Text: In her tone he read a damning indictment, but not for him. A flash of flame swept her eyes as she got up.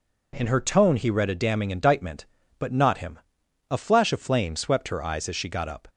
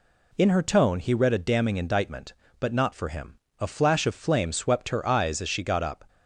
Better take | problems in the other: second | skips "for"; at 2.9 s

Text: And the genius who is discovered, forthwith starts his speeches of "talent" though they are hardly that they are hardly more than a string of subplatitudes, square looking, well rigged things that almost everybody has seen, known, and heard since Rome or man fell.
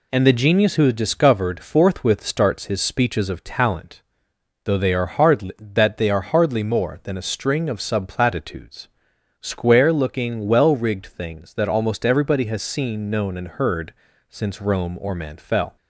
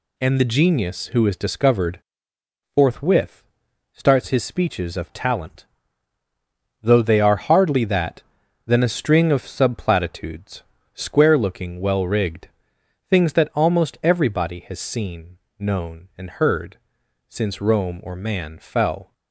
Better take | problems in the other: first | pauses between "forthwith" and "starts"; noticeable; at 3.4 s; 0.50 s long // pauses between "talent" and "though"; at 5.6 s; 1.1 s long; noticeable in the first // skips "they are hardly more"; at 8.4 s // pauses between "rigged" and "things"; noticeable; at 12.4 s; 0.62 s long // pauses between "heard" and "since"; noticeable; at 16.7 s; 0.50 s long; slight in the first

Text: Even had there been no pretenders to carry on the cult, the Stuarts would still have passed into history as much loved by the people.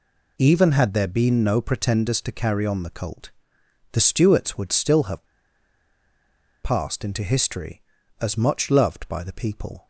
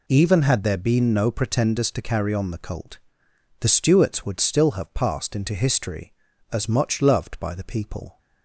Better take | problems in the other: second | pauses between "have" and "passed"; strong; at 5.2 s; 1.3 s long

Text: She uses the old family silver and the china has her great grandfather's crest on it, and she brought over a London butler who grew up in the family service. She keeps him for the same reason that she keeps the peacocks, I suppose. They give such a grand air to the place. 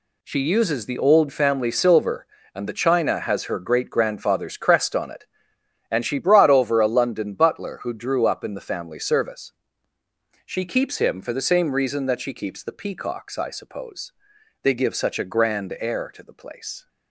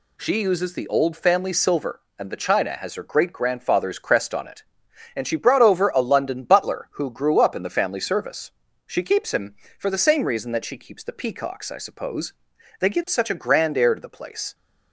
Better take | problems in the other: second | says "drew" for "grew"; at 7.9 s

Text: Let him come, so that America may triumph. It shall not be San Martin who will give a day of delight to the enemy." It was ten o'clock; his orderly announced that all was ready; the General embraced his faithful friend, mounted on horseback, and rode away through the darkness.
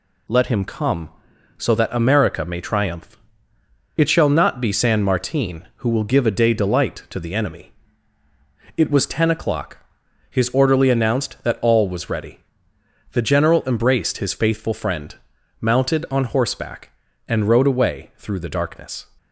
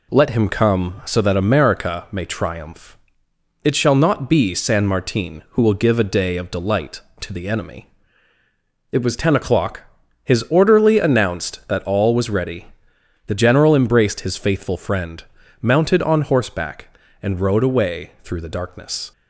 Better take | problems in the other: second | skips "of"; at 6.5 s

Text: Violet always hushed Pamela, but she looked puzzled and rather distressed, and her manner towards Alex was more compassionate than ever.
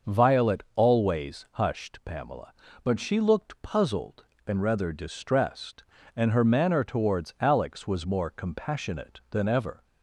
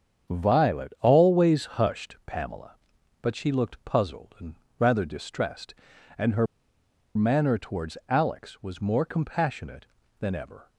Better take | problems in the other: first | starts louder than the rest; strong; until 1.3 s; 8 dB; also in the first // pauses between "and" and "rather"; slight; at 4.5 s; 0.22 s long // pauses between "her" and "manner"; noticeable; at 6.4 s; 0.69 s long

